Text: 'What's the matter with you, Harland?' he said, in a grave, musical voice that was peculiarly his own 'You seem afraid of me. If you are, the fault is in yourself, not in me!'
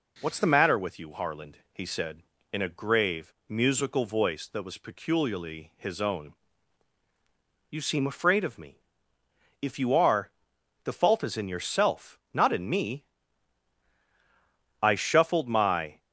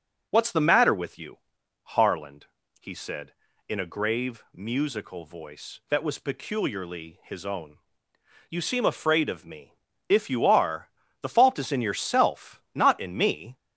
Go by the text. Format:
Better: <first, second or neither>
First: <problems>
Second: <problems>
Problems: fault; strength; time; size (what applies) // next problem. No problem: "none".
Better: second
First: pauses between "own" and "You"; strong; at 6.3 s; 1.3 s long // goes on to say "I shuffled my"; noticeable; from 14.8 s on; 1.1 s long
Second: pauses between "own" and "You"; noticeable; at 7.7 s; 0.72 s long